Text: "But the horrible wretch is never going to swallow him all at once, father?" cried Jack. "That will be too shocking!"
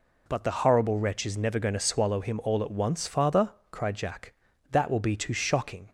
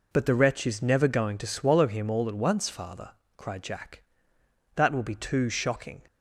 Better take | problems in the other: first | skips "horrible"; at 0.3 s

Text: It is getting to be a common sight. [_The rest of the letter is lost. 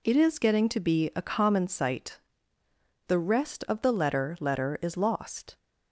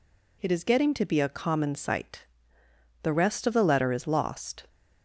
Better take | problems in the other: second | says "letter" twice; at 4.3 s

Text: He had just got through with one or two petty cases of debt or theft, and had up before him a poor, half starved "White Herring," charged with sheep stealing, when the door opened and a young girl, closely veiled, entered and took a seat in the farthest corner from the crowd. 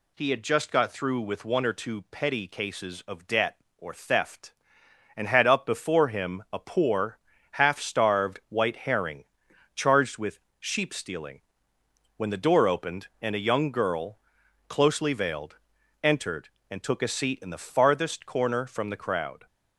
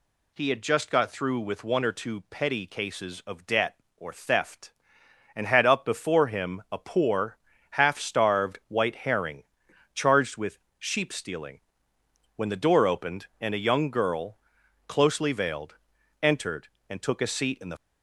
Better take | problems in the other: first | pauses between "with" and "sheep"; slight; at 10.5 s; 0.22 s long; slight in the first // stops before "farthest corner from the crowd"; at 17.7 s

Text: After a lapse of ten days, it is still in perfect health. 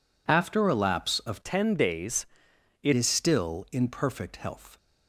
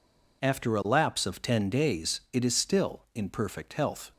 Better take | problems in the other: second | changes voice from "ten" to "it"; from 1.4 to 2.9 s; 1.5 s long

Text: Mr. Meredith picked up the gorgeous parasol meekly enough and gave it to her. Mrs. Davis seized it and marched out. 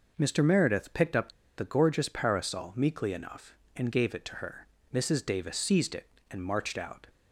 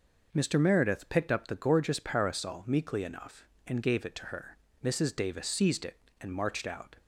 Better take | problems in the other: second | pauses between "up" and "the"; slight; at 1.3 s; 0.25 s long

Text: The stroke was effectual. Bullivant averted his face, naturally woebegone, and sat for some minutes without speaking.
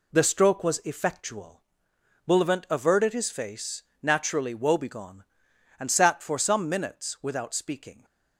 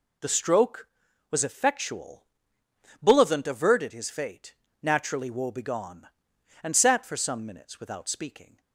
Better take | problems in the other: first | says "fate" for "face"; at 4.1 s

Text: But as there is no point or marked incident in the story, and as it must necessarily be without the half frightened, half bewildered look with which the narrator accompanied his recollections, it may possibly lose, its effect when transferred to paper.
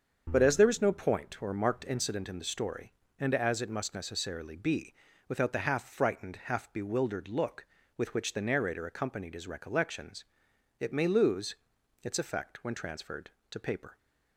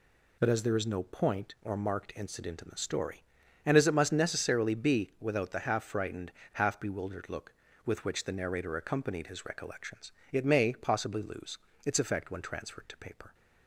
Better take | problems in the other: second | starts louder than the rest; until 1.3 s; 7 dB // pauses between "be" and "without"; slight; at 4.9 s; 0.34 s long // skips "possibly"; at 11.0 s

